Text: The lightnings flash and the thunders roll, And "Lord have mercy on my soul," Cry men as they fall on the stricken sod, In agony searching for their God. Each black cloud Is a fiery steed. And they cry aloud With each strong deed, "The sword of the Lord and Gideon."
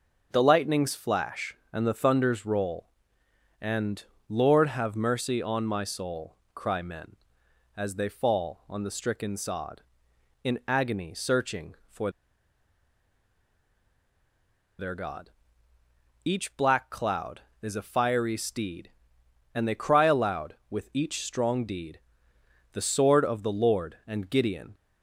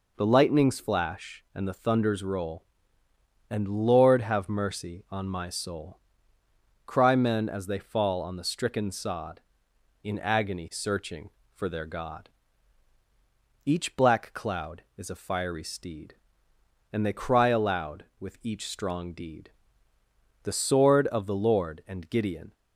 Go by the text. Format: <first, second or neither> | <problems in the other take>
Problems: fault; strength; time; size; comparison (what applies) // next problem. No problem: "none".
second | pauses between "And" and "Lord"; slight; at 4.0 s; 0.28 s long // pauses between "for" and "their"; strong; at 12.0 s; 2.6 s long